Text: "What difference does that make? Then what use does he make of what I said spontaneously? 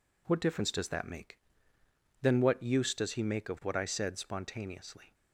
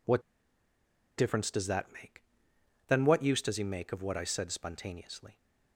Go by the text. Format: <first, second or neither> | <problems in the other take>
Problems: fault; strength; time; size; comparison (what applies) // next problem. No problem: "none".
first | pauses between "What" and "difference"; noticeable; at 0.2 s; 0.96 s long